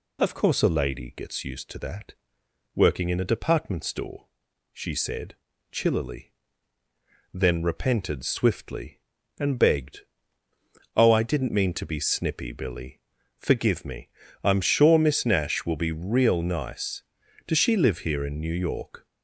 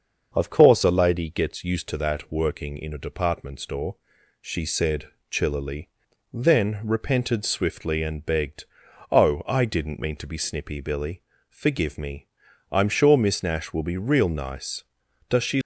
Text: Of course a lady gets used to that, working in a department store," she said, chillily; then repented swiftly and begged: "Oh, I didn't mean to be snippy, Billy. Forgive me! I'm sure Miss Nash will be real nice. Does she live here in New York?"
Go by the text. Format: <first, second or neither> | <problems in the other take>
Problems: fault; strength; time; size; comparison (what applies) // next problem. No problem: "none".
first | starts louder than the rest; until 1.3 s; 6.5 dB // stops before "live here in New York"; at 15.6 s